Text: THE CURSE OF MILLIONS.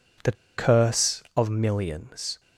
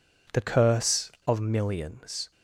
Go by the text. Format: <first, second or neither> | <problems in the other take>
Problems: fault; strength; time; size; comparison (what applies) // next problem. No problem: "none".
second | pauses between "THE" and "CURSE"; slight; at 0.3 s; 0.23 s long